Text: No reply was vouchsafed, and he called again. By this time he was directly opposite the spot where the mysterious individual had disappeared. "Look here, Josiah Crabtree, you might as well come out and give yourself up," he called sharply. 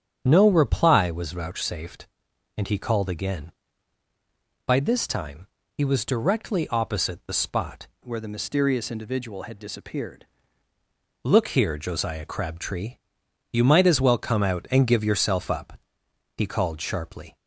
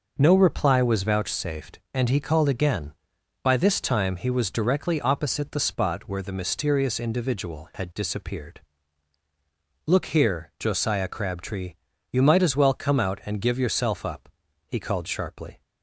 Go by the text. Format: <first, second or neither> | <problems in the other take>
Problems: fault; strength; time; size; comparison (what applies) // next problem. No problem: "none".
second | starts louder than the rest; strong; until 1.2 s; 9 dB // pauses between "time" and "he"; slight; at 5.4 s; 0.28 s long // changes voice from "where" to "disappeared"; from 8.0 to 10.2 s; 2.2 s long